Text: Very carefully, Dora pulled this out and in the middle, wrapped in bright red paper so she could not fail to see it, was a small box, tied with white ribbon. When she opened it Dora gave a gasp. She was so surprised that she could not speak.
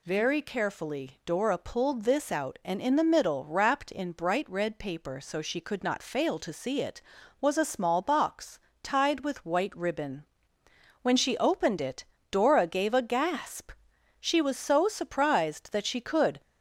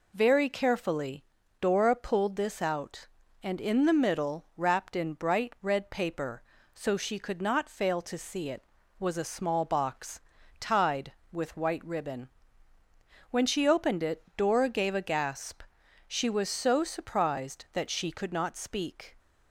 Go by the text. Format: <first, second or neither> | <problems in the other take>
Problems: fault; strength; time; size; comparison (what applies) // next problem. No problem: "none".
second | pauses between "it" and "Dora"; slight; at 12.0 s; 0.28 s long // stops before "not speak"; at 16.4 s